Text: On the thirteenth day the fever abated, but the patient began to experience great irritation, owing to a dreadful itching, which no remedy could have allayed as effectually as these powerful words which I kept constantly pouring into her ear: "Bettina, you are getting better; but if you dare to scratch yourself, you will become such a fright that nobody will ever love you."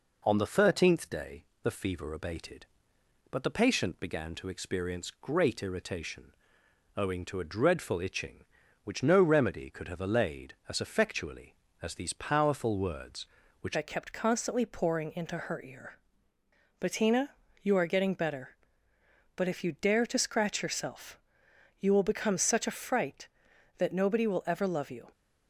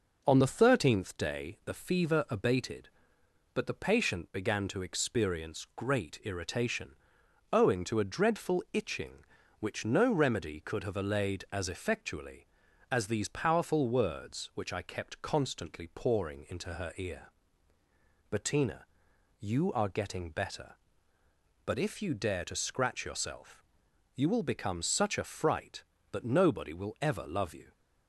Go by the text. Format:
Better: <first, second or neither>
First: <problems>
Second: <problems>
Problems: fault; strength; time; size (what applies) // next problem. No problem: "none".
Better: second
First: pauses between "day" and "the"; slight; at 1.4 s; 0.20 s long // changes voice at "I"; from 13.7 s on; 11.3 s long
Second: none